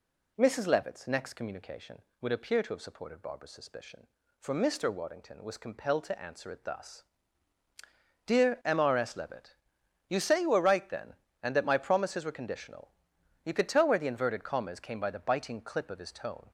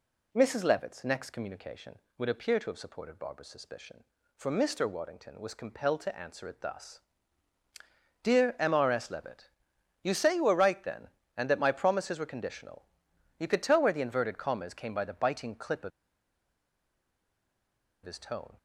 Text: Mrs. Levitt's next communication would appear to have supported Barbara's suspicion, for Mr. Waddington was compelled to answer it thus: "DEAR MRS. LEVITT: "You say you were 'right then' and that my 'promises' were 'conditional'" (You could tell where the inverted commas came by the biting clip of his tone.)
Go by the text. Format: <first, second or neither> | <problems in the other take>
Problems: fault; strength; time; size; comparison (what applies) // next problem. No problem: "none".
first | pauses between "of" and "his"; strong; at 15.9 s; 2.1 s long